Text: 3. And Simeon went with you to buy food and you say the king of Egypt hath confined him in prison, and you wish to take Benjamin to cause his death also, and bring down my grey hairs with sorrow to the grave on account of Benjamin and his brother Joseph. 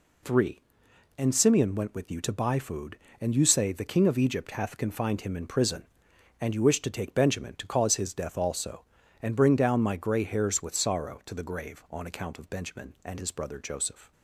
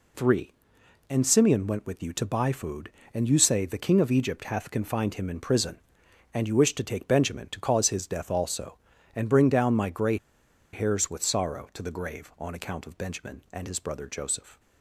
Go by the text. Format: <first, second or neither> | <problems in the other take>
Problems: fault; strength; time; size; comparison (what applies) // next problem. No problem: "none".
first | pauses between "grey" and "hairs"; noticeable; at 10.1 s; 0.57 s long